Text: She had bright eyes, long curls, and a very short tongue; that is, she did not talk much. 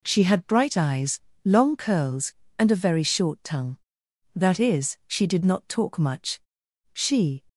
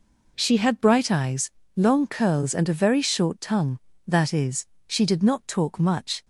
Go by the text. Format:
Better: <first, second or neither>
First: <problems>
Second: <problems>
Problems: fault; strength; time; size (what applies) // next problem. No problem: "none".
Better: second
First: goes on to say "She"; from 6.9 s on; 0.52 s long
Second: none